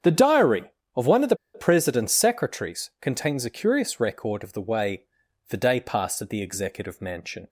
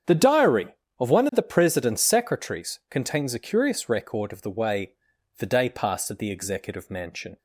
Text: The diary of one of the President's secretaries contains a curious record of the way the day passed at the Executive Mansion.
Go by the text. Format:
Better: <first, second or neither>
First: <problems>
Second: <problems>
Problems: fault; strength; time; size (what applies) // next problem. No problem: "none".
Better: second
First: starts louder than the rest; strong; until 1.5 s; 8 dB // pauses between "the" and "President's"; slight; at 1.3 s; 0.19 s long // pauses between "way" and "the"; noticeable; at 5.0 s; 0.48 s long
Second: starts louder than the rest; strong; until 1.4 s; 8 dB // pauses between "way" and "the"; noticeable; at 4.9 s; 0.48 s long